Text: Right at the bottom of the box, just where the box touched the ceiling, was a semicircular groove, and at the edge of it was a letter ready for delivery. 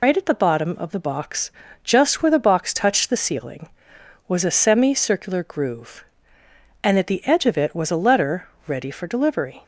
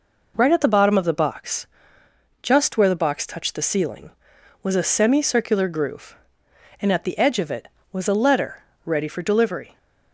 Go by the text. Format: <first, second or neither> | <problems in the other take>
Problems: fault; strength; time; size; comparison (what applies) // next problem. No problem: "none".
second | loses the start of "Right"; at 0.0 s; 135 ms // pauses between "letter" and "ready"; slight; at 8.4 s; 0.20 s long; slight in the second